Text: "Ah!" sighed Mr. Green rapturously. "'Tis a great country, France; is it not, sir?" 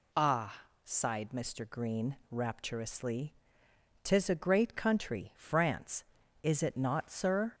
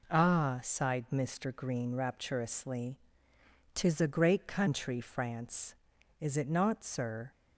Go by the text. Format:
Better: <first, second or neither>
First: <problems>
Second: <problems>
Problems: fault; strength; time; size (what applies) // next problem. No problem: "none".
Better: neither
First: none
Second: none